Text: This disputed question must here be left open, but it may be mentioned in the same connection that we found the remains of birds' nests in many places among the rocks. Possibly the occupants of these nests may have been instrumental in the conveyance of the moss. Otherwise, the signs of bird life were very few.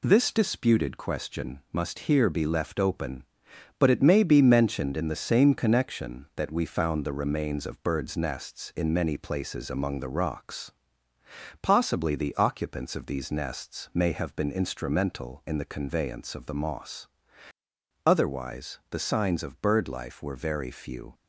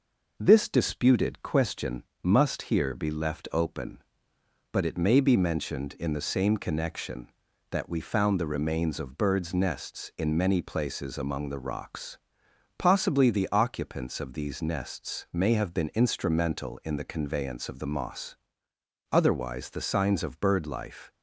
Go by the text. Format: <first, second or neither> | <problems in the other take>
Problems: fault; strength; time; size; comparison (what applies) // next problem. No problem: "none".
first | pauses between "question" and "must"; slight; at 2.0 s; 0.20 s long // stops before "were very few"; at 21.1 s